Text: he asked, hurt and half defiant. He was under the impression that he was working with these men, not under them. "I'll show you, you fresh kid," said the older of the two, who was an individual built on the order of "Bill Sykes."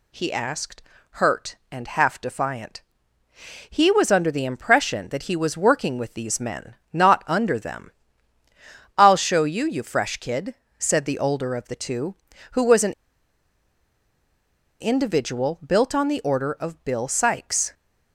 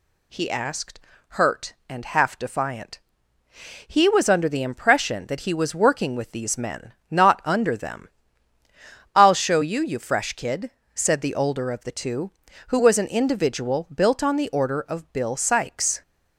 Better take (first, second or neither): second